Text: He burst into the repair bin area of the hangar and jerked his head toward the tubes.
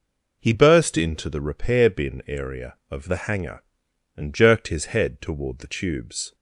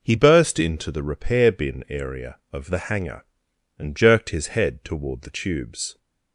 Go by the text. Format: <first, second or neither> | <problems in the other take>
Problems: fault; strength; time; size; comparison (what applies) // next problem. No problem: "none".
neither | none